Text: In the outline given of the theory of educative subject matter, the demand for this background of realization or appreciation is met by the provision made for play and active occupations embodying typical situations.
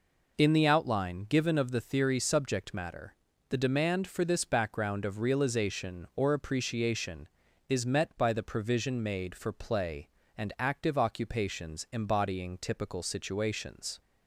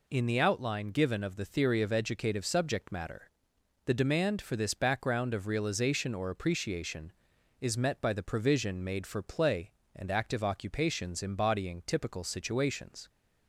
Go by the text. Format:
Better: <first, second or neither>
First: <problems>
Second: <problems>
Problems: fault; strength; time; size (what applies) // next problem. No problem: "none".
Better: second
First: skips "of educative"; at 2.1 s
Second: none